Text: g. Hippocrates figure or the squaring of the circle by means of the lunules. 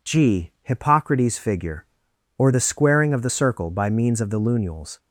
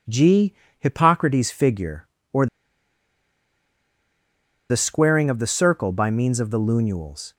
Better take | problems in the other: first | pauses between "or" and "the"; strong; at 2.4 s; 2.2 s long

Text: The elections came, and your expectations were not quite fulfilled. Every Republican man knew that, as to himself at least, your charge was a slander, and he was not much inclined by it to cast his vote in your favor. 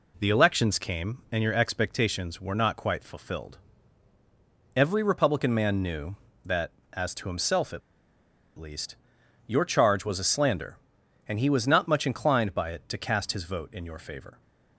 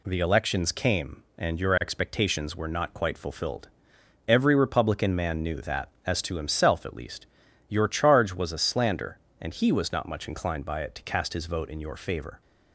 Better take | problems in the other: second | pauses between "at" and "least"; noticeable; at 7.8 s; 0.78 s long

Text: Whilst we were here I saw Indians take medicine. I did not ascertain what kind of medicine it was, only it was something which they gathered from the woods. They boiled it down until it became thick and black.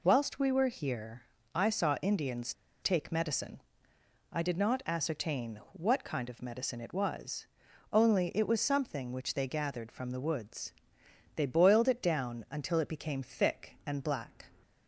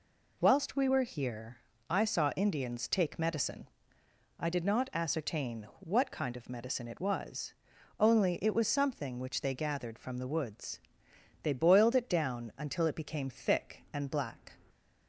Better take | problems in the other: second | pauses between "here" and "I"; slight; at 1.2 s; 0.34 s long; slight in the second // pauses between "Indians" and "take"; slight; at 2.5 s; 0.28 s long

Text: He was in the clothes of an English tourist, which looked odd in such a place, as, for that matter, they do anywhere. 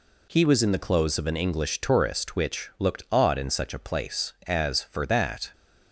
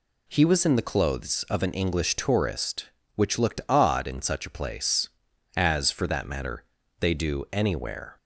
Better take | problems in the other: second | stops before "matter they do anywhere"; at 5.5 s

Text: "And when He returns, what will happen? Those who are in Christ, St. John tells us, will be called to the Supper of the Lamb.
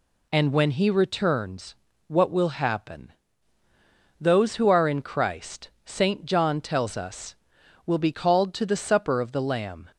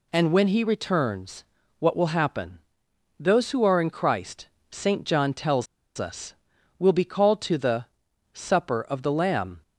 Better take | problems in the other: first | pauses between "tells" and "us"; slight; at 5.6 s; 0.31 s long // pauses between "the" and "Supper"; noticeable; at 7.8 s; 0.48 s long

